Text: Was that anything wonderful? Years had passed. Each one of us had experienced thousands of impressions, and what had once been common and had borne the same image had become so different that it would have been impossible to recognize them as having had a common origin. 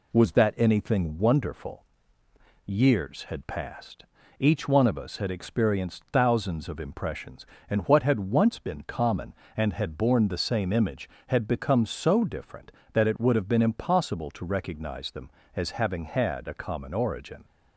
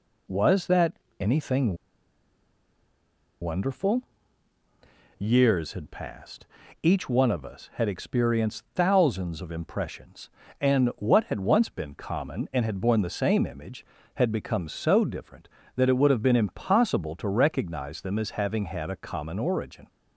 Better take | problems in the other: first | pauses between "that" and "anything"; slight; at 0.9 s; 0.26 s long // pauses between "anything" and "wonderful"; strong; at 1.7 s; 1.6 s long

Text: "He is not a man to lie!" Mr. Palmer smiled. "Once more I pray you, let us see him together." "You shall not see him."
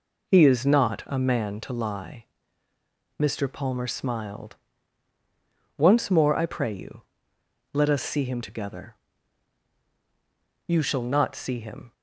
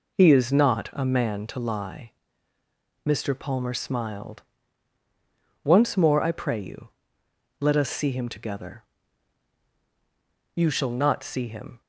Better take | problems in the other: neither | none

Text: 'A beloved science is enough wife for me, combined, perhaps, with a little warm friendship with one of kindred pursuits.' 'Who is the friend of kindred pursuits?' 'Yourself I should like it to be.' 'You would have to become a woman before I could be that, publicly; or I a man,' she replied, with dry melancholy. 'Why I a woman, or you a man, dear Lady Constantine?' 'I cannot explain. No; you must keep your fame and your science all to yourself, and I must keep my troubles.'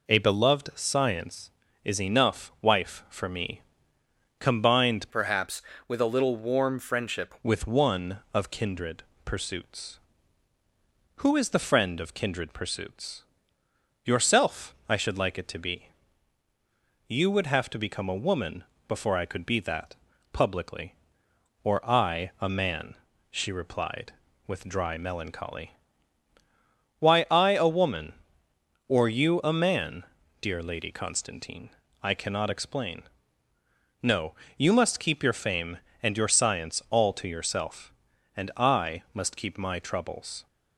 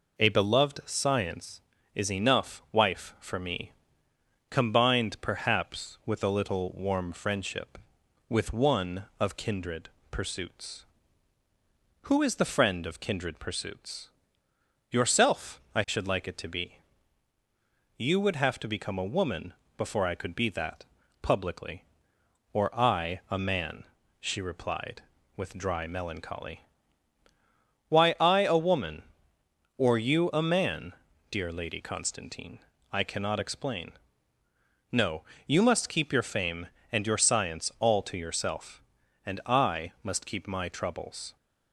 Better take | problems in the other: second | changes voice from "perhaps" to "friendship"; from 5.1 to 7.3 s; 2.2 s long // pauses between "kindred" and "pursuits"; slight; at 9.0 s; 0.22 s long; slight in the second // pauses between "woman" and "before"; slight; at 18.6 s; 0.24 s long; slight in the second

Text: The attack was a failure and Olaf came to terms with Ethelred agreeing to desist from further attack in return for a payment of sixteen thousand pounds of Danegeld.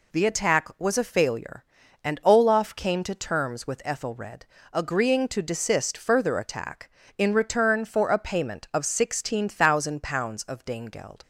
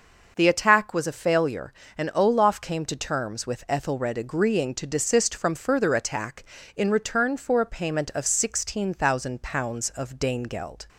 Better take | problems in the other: second | pauses between "Ethelred" and "agreeing"; slight; at 4.4 s; 0.28 s long // skips "from"; at 5.9 s

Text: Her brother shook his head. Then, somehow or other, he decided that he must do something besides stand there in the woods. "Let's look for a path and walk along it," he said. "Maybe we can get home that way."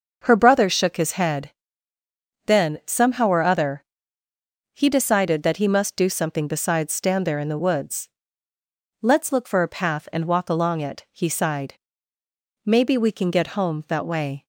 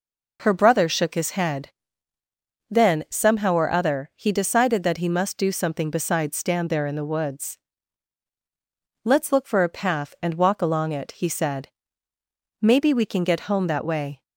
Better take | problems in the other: second | starts louder than the rest; until 1.2 s; 6.5 dB // says "sighed" for "said"; at 11.2 s

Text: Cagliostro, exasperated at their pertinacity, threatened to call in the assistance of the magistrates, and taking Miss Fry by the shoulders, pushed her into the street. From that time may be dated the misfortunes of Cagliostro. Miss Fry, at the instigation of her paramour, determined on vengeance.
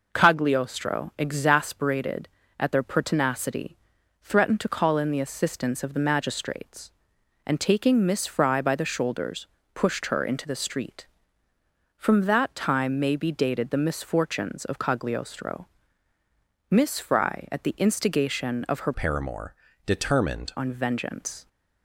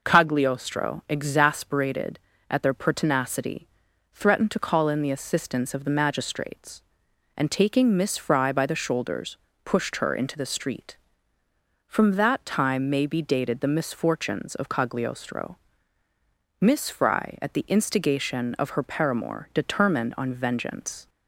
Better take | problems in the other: second | changes voice from "paramour" to "determined"; from 18.9 to 20.5 s; 1.6 s long

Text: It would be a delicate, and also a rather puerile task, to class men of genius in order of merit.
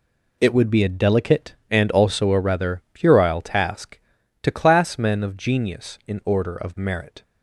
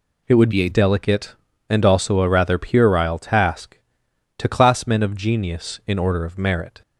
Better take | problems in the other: first | changes voice from "be" to "a"; from 0.5 to 0.6 s; 0.1 s long

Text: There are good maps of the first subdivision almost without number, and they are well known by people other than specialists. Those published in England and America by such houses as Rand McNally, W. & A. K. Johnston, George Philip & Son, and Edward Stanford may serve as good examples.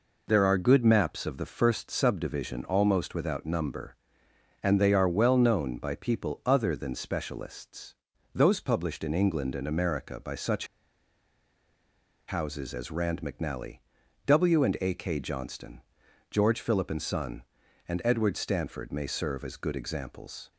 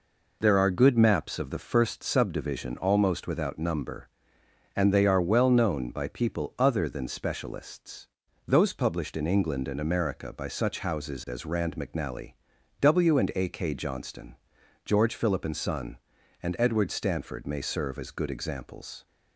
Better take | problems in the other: second | pauses between "such" and "houses"; strong; at 10.6 s; 1.6 s long

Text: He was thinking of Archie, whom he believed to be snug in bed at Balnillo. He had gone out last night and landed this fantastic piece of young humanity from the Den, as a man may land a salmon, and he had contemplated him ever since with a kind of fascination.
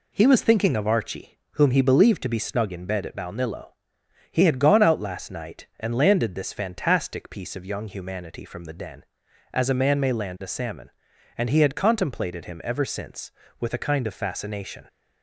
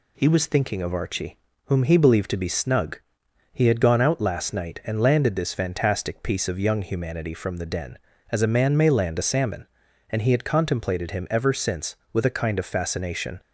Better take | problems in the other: first | skips "in bed at Balnillo"; at 3.2 s

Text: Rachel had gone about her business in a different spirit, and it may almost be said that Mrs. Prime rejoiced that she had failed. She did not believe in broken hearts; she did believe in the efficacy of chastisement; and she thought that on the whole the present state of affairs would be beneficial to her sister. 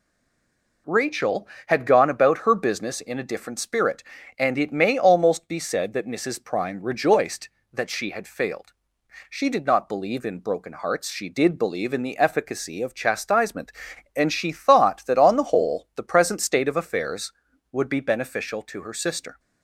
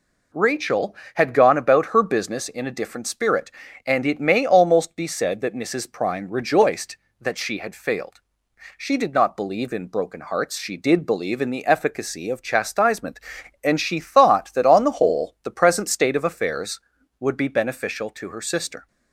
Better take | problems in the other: second | stays silent before the first word; slight; until 0.8 s; 0.8 s long

